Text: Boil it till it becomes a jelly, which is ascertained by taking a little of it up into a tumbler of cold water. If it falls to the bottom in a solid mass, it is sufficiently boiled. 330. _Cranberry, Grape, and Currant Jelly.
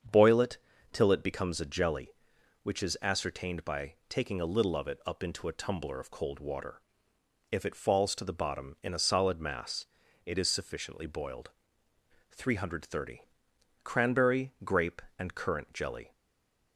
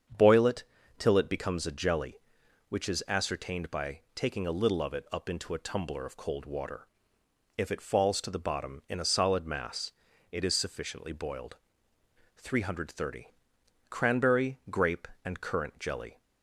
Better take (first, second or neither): second